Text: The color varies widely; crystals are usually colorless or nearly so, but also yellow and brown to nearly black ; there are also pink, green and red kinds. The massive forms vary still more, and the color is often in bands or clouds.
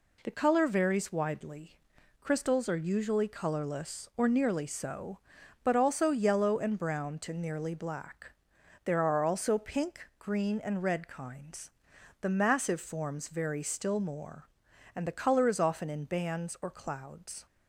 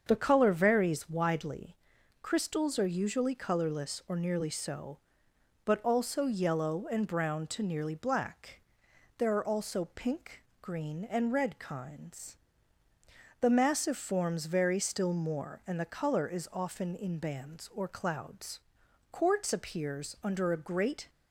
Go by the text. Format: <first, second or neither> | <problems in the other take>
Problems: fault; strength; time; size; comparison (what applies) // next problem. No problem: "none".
first | starts louder than the rest; until 1.0 s; 7 dB // goes on to say "Quartz appears under a great"; strong; from 19.1 s on; 1.9 s long